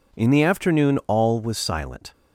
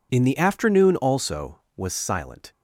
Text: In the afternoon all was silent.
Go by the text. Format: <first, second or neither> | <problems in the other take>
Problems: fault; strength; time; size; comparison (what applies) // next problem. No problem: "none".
first | says "also" for "all"; at 0.9 s